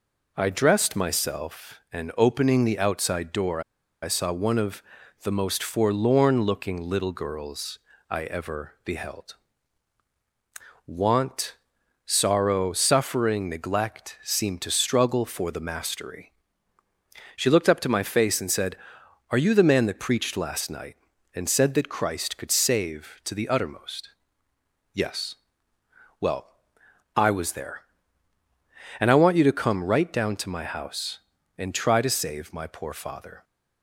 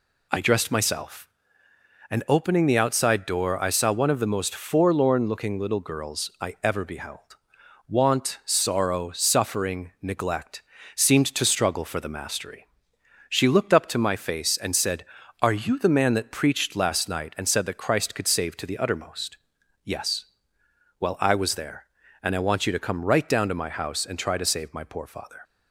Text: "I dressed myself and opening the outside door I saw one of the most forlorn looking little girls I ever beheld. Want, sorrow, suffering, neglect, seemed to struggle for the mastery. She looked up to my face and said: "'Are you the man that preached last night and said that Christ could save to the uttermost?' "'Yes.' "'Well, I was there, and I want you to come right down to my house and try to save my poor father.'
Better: second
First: pauses between "door" and "I"; at 3.6 s; 0.42 s long // pauses between "of" and "the"; at 4.8 s; 0.42 s long // pauses between "girls" and "I"; slight; at 7.7 s; 0.32 s long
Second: none

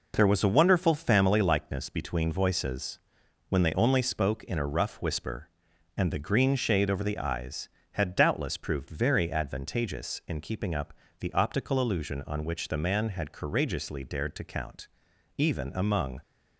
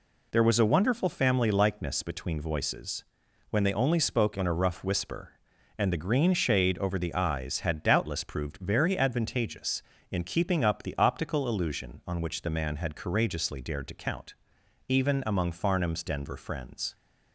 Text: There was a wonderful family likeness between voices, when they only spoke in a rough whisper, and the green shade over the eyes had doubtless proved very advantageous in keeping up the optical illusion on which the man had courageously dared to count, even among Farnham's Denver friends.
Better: second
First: pauses between "up" and "the"; slight; at 10.9 s; 0.24 s long // stops before "Farnham's Denver friends"; at 16.2 s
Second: none

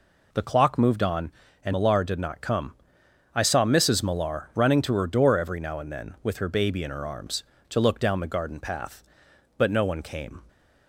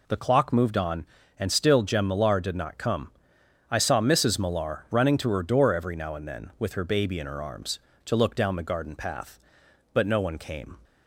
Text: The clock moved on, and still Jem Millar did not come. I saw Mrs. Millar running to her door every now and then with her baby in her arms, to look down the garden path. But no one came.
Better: second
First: skips "still Jem"; at 1.7 s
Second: none

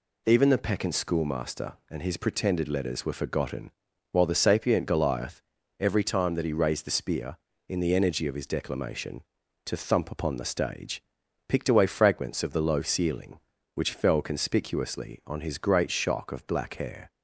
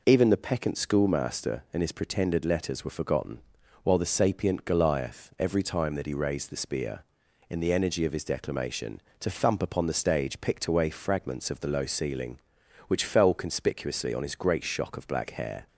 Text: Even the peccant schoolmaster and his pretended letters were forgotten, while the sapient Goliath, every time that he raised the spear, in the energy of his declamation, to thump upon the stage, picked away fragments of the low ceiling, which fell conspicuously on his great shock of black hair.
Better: neither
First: none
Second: none

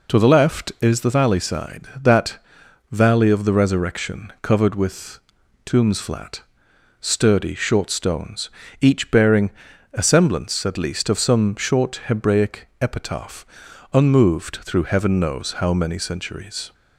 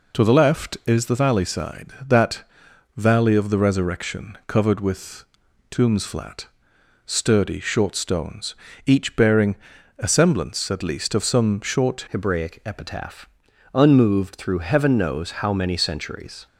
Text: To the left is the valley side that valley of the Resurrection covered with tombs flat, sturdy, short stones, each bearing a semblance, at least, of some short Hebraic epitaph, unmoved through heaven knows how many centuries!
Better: first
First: pauses between "that" and "valley"; noticeable; at 2.3 s; 0.54 s long // pauses between "with" and "tombs"; noticeable; at 5.1 s; 0.46 s long // pauses between "bearing" and "a"; at 9.4 s; 0.44 s long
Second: pauses between "that" and "valley"; noticeable; at 2.4 s; 0.54 s long // pauses between "with" and "tombs"; noticeable; at 5.2 s; 0.46 s long // pauses between "bearing" and "a"; at 9.5 s; 0.44 s long // changes voice at "Hebraic"; from 12.0 s on; 4.4 s long

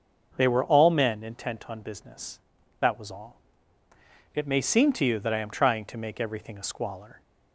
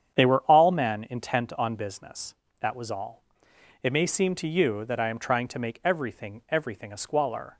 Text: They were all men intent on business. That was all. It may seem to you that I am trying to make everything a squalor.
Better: first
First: starts louder than the rest; noticeable; until 1.3 s; 6 dB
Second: starts louder than the rest; strong; until 1.2 s; 8.5 dB // says "everything" twice; at 6.4 s

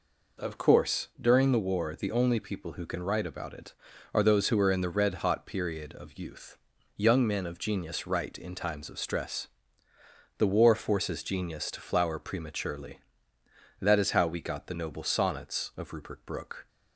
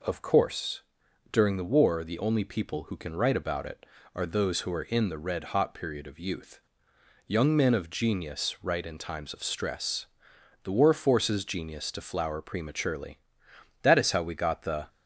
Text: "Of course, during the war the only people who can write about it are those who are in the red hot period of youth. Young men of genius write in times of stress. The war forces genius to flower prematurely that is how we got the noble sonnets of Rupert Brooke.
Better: first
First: none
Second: stops before "noble sonnets of Rupert Brooke"; at 14.8 s

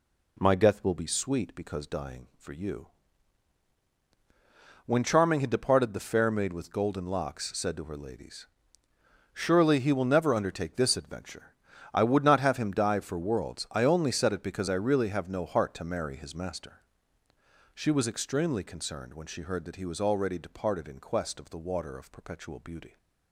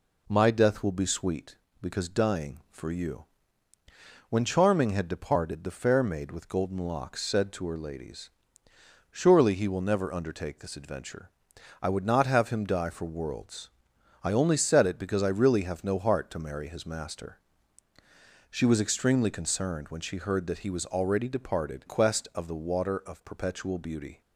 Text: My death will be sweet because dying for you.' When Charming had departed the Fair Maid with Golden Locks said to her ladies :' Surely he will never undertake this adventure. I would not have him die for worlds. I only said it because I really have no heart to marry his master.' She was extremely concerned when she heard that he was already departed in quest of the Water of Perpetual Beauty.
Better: first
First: none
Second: skips "in"; at 21.8 s

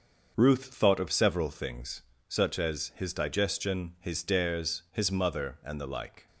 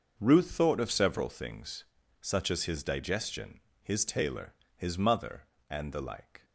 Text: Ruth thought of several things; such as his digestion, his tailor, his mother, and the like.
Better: second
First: starts louder than the rest; until 1.3 s; 6 dB // says "dares" for "tailor"; at 4.2 s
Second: starts louder than the rest; noticeable; until 1.1 s; 6 dB

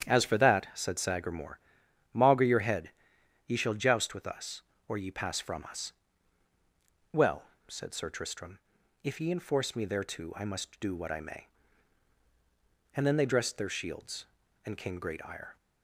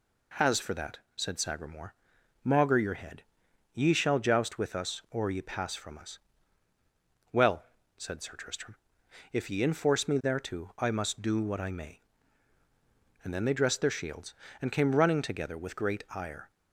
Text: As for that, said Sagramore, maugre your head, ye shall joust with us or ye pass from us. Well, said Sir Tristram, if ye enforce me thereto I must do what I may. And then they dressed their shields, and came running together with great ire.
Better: second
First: starts louder than the rest; strong; until 1.1 s; 9 dB // skips "running together with"; at 14.9 s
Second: none

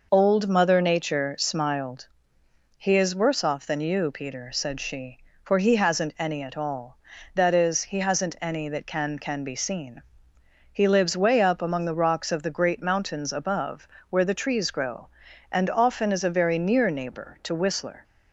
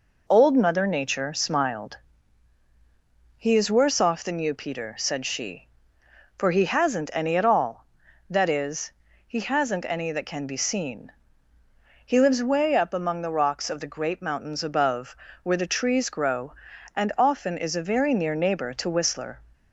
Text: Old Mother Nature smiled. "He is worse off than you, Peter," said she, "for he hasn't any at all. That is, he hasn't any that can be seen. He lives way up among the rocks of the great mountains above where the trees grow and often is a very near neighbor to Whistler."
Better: second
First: says "can" twice; at 9.1 s // pauses between "above" and "where"; slight; at 13.8 s; 0.24 s long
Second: pauses between "above" and "where"; slight; at 15.1 s; 0.28 s long

